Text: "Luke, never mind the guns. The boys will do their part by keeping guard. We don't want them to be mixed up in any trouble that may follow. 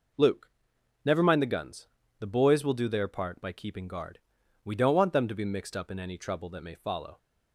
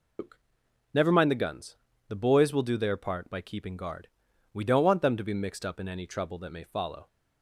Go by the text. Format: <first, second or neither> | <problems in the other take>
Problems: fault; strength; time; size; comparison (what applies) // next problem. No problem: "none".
first | loses the start of "Luke"; at 0.1 s; 150 ms